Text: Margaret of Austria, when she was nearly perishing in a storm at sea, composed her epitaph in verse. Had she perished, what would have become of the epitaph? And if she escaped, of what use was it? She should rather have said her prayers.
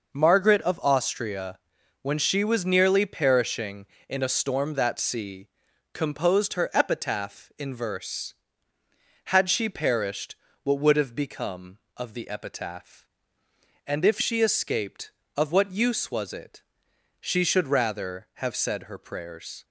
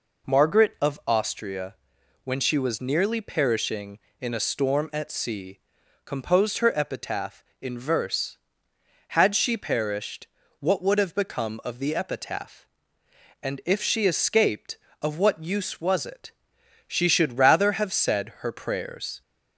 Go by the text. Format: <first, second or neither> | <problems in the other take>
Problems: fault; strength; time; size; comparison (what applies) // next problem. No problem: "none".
second | says "that" for "at"; at 4.7 s